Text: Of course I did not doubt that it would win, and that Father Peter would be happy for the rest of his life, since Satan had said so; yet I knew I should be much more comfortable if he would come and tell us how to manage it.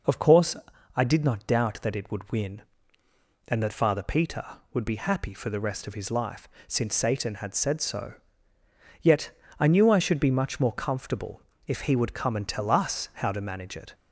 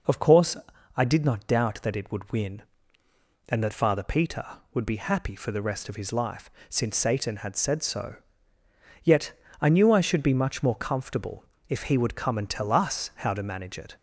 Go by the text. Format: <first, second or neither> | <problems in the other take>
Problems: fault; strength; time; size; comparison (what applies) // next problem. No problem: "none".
neither | pauses between "course" and "I"; the same in both // pauses between "yet" and "I"; slight; the same in both // pauses between "comfortable" and "if"; slight; the same in both